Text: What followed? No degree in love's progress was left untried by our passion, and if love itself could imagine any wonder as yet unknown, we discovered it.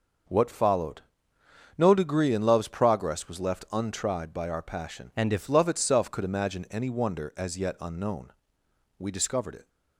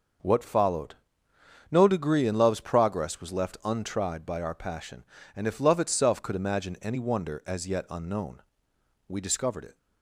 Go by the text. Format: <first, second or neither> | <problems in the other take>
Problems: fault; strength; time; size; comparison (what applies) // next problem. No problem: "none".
second | starts louder than the rest; noticeable; until 2.0 s; 6 dB; also in the second // changes voice from "and" to "if"; from 5.1 to 5.4 s; 0.3 s long